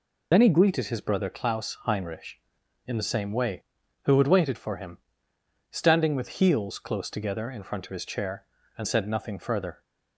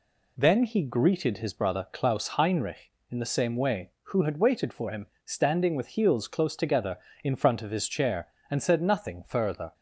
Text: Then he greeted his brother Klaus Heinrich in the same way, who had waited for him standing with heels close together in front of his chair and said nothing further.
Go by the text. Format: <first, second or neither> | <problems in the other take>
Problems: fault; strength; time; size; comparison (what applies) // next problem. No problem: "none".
second | loses the start of "Then"; at 0.3 s; 40 ms // pauses between "him" and "standing"; noticeable; at 4.9 s; 0.72 s long; slight in the second